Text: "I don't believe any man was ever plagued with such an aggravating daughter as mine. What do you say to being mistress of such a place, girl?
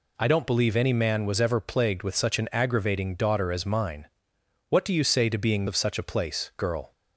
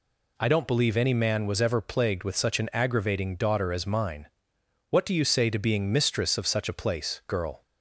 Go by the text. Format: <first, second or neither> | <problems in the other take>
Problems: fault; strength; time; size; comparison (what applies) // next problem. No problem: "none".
second | skips "mistress"; at 5.6 s